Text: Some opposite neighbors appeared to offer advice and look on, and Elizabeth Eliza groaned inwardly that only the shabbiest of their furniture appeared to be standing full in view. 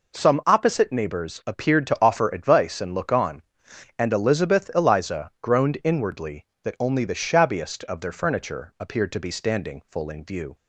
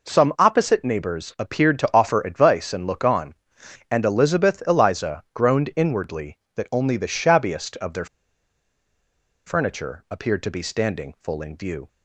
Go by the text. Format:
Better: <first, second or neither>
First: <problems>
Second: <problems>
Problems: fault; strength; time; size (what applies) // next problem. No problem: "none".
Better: first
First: none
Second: pauses between "their" and "furniture"; strong; at 8.0 s; 1.4 s long